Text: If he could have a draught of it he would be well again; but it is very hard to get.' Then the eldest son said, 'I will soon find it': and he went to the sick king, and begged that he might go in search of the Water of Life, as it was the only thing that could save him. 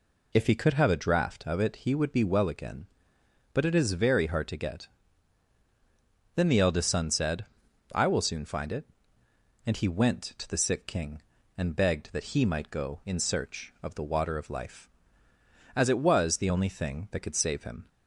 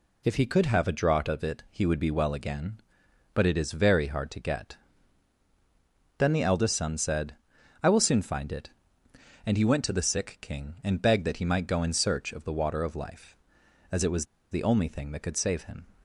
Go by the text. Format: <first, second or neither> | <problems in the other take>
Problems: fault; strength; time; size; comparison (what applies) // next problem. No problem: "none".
first | pauses between "was" and "the"; slight; at 14.2 s; 0.27 s long